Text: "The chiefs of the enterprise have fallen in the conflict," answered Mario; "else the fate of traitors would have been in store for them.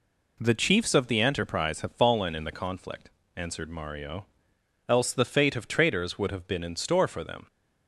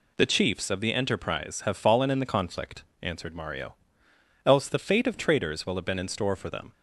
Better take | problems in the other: first | says "will" for "would"; at 5.6 s

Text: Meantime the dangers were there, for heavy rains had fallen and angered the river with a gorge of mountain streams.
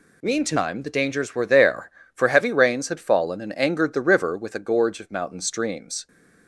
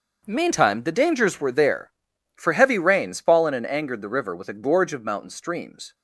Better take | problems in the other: first | starts louder than the rest; until 1.2 s; 6.5 dB // skips "had"; at 3.1 s

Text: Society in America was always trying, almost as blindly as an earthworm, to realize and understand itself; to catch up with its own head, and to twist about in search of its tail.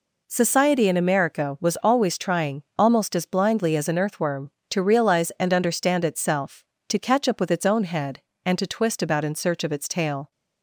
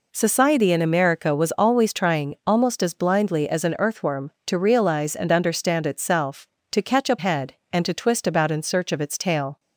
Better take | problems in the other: first | skips "with its own"; at 7.1 s

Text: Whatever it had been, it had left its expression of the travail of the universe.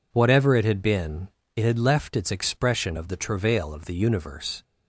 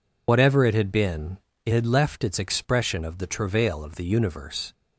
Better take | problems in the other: first | loses the start of "Whatever"; at 0.2 s; 60 ms

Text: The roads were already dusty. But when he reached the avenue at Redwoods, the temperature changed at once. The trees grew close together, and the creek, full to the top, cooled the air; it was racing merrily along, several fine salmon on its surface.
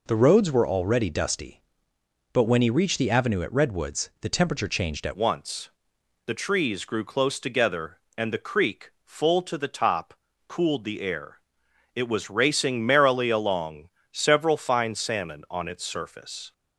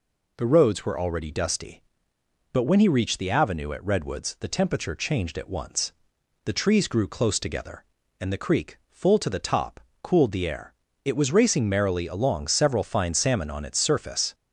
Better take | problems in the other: second | changes voice at "once"; from 5.1 s on; 11.4 s long

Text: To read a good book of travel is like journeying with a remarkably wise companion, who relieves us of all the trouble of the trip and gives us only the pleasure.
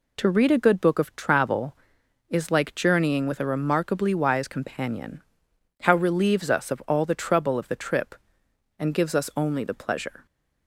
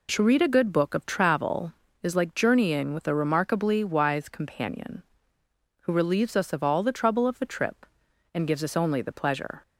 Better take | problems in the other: second | says "how" for "who"; at 5.8 s

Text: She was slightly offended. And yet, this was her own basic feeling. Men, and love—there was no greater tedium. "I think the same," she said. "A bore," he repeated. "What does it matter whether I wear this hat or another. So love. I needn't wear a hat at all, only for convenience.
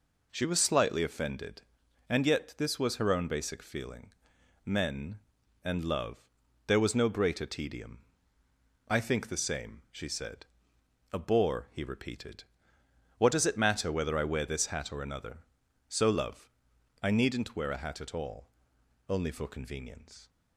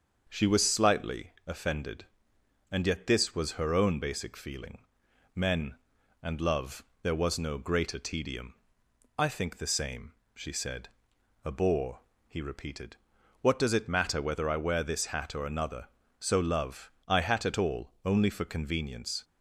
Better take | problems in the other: first | starts louder than the rest; until 1.3 s; 6.5 dB // skips "needn't wear a"; at 17.2 s

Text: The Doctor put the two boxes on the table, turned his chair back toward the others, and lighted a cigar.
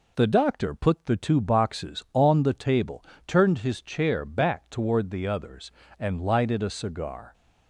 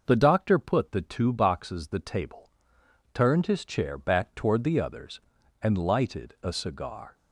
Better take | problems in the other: first | skips "on"; at 1.8 s

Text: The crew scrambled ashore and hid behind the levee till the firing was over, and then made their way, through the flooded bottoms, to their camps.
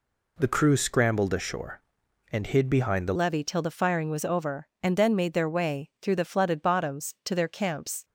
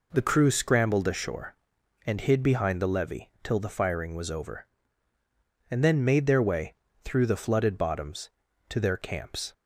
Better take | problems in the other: second | changes voice at "levee"; from 3.1 s on; 4.9 s long

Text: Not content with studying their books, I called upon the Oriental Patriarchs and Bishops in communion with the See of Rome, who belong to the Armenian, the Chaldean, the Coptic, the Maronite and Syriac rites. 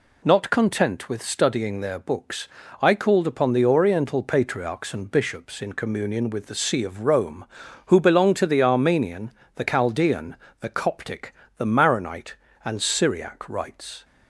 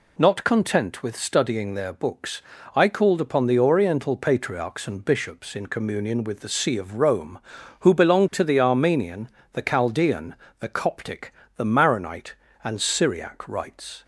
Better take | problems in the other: neither | none

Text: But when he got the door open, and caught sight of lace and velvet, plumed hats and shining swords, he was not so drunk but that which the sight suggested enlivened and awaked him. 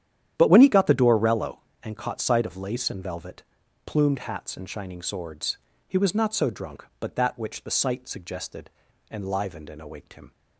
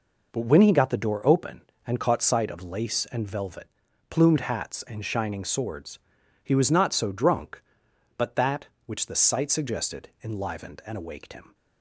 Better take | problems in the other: second | starts louder than the rest; strong; until 1.3 s; 10.5 dB // says "rello" for "open"; at 1.1 s // pauses between "suggested" and "enlivened"; at 8.6 s; 0.42 s long

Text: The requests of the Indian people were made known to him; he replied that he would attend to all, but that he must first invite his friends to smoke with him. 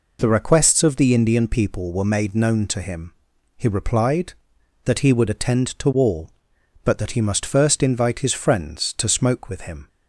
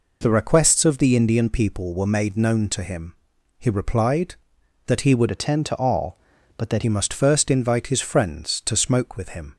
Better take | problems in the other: first | changes voice from "attend" to "that"; from 5.3 to 6.8 s; 1.5 s long

